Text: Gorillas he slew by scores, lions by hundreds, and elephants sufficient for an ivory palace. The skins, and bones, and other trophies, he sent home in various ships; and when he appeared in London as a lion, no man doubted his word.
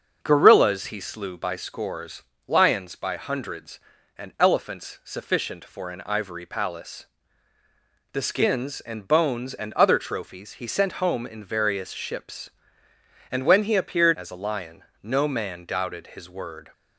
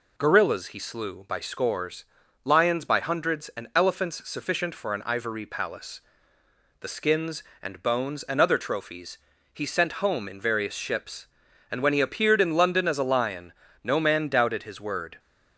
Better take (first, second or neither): second